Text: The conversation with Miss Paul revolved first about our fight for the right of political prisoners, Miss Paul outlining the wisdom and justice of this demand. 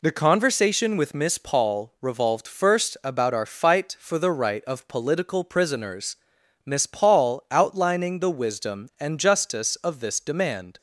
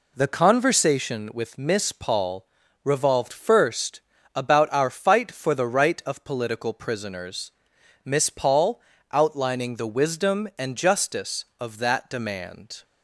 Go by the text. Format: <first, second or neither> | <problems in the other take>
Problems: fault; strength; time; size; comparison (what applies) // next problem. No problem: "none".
first | pauses between "Paul" and "revolved"; at 2.4 s; 0.38 s long // pauses between "first" and "about"; slight; at 4.0 s; 0.34 s long // pauses between "Paul" and "outlining"; slight; at 8.8 s; 0.30 s long // says "that" for "this"; at 11.7 s